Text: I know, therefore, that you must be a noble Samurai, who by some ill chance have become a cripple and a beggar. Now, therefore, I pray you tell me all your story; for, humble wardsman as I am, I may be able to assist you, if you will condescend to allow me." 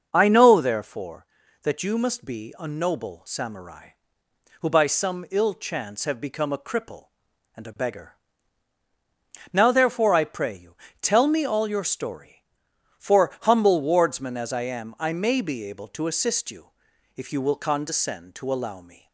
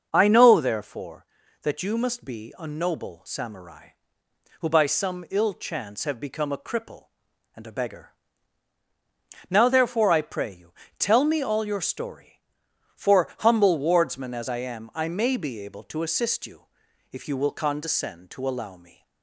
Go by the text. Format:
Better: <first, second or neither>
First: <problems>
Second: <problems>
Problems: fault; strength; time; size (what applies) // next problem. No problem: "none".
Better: neither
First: pauses between "you" and "tell"; slight; at 10.7 s; 0.26 s long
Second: pauses between "you" and "tell"; slight; at 10.7 s; 0.26 s long